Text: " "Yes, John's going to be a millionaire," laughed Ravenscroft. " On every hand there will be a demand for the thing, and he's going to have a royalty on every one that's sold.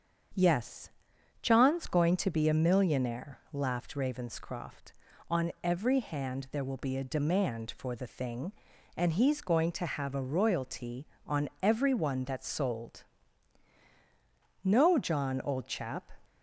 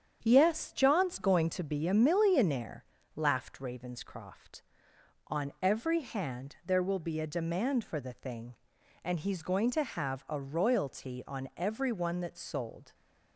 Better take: second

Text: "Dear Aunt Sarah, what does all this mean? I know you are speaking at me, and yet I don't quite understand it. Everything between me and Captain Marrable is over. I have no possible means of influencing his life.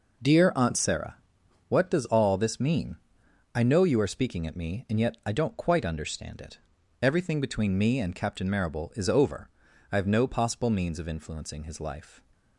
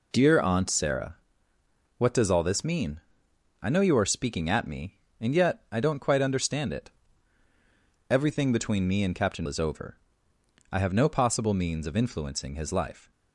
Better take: first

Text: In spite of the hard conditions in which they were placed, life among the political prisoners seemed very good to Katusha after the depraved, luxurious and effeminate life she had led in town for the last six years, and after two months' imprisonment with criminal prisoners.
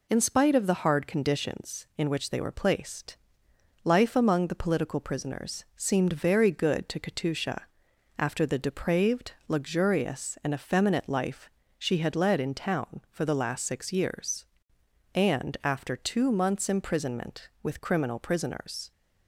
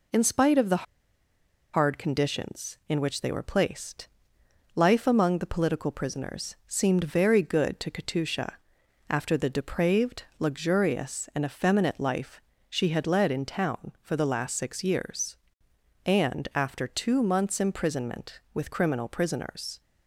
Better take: first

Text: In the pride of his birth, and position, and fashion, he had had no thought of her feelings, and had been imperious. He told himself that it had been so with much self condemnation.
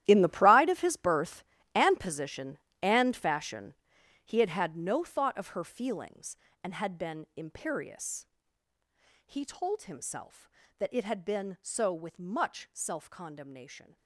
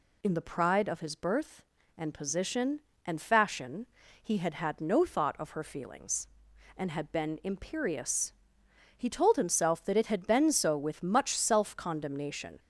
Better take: second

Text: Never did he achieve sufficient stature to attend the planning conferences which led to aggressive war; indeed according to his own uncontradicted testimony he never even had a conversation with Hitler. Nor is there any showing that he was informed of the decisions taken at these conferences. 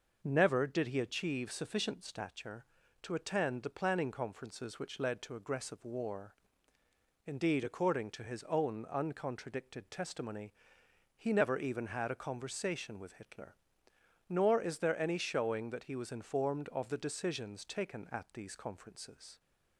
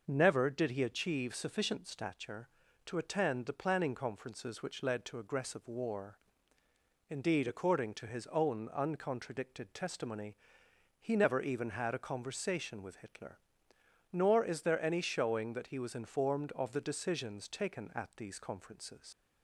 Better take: first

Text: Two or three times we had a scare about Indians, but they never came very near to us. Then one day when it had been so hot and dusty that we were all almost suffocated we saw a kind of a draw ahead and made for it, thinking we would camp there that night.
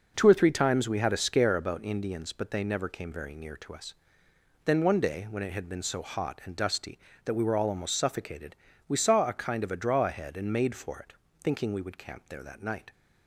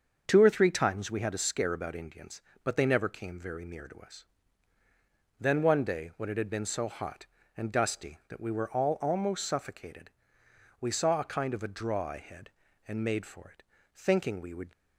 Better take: first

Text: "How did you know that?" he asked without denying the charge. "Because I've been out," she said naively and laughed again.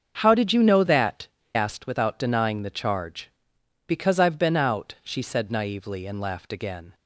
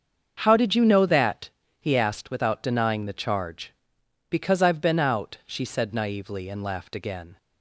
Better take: second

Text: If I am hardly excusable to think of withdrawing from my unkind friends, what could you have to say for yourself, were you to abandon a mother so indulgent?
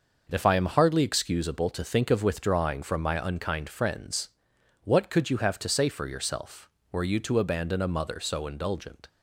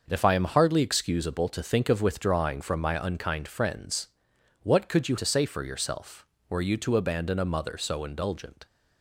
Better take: first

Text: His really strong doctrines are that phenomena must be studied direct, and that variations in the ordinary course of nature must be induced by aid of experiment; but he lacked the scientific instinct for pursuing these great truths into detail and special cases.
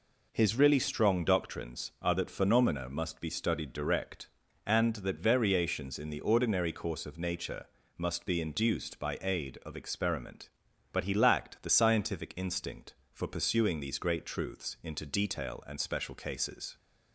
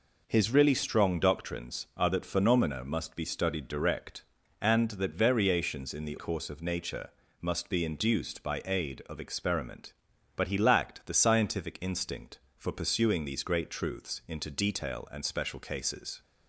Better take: first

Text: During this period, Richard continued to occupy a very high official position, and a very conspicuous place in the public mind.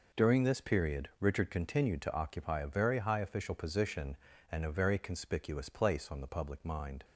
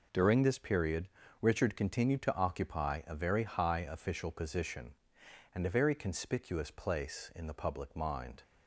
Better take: second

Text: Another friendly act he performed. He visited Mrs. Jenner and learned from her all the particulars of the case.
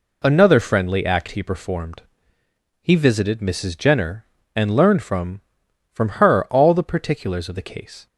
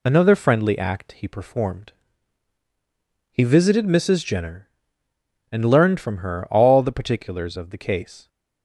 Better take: second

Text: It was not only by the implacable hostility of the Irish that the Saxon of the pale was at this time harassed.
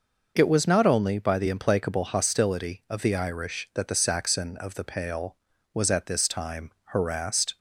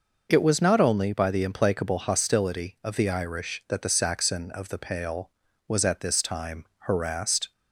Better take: neither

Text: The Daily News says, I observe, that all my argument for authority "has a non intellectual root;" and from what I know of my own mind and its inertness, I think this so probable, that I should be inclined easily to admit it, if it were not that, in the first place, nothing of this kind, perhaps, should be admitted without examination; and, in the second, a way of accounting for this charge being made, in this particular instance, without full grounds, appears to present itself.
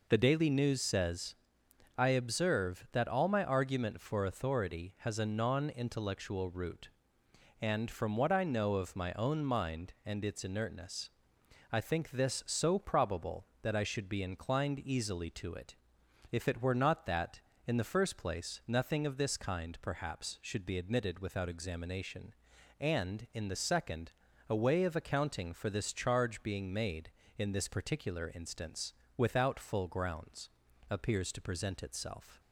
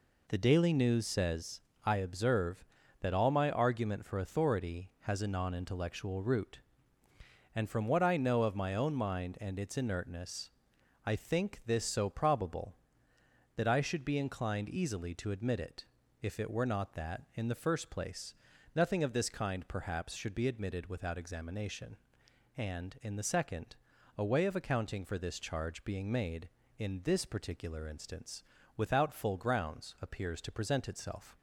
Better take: second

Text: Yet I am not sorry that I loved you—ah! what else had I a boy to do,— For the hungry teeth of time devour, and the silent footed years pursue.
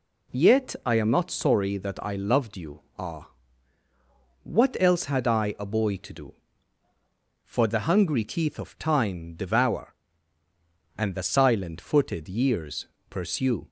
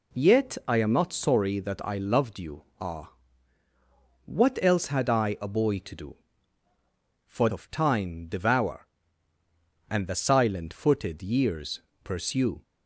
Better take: first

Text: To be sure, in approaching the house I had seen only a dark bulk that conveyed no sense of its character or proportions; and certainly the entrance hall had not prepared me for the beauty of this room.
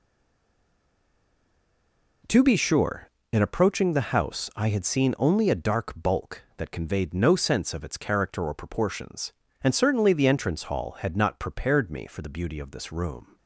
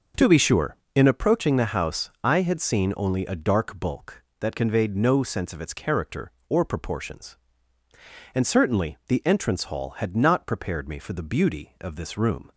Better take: second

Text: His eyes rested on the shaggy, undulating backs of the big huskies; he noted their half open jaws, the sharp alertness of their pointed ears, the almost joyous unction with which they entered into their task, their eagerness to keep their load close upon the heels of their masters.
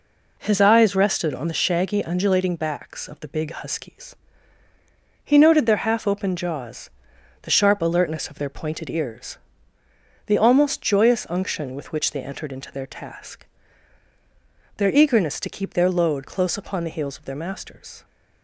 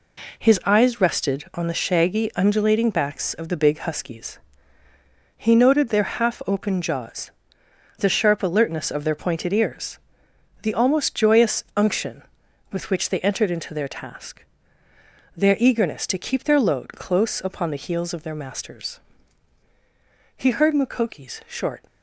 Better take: first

